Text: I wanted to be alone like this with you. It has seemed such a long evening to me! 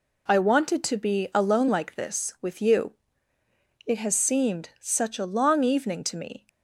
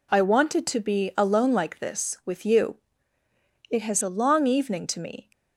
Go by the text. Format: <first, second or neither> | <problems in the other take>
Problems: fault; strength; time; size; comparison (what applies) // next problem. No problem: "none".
first | skips "seemed such"; at 4.0 s